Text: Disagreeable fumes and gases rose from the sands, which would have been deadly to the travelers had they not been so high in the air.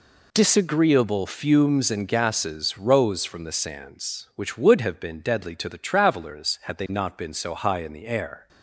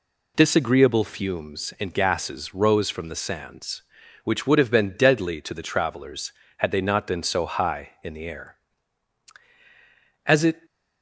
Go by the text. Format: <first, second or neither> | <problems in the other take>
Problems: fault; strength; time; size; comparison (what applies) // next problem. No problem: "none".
first | goes on to say "As it"; slight; from 10.2 s on; 0.40 s long